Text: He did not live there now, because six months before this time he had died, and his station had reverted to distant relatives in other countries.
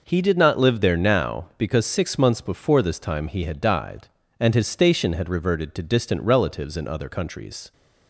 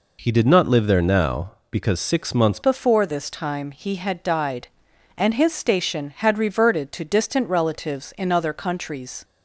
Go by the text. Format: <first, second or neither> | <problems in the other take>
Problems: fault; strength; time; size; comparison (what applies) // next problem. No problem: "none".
first | changes voice at "before"; from 2.6 s on; 6.6 s long